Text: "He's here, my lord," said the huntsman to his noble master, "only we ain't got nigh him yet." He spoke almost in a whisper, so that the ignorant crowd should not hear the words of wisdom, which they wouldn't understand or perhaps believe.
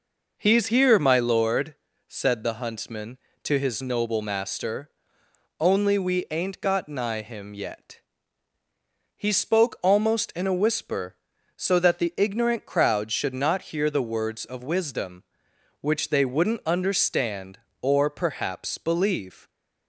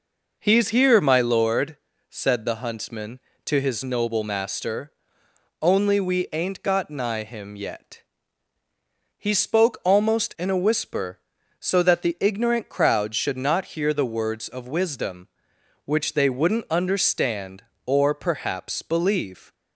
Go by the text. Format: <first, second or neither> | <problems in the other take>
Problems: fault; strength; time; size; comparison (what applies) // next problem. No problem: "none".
neither | none